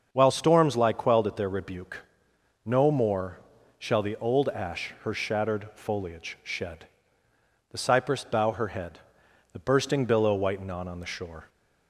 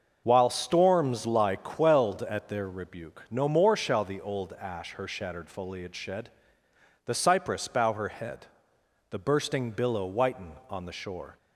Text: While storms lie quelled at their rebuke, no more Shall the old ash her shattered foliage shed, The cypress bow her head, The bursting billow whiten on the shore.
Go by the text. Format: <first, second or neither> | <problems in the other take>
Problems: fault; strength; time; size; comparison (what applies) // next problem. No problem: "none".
second | starts louder than the rest; until 1.1 s; 6.5 dB; also in the second // pauses between "more" and "Shall"; at 3.3 s; 0.42 s long // says "on" twice; at 10.8 s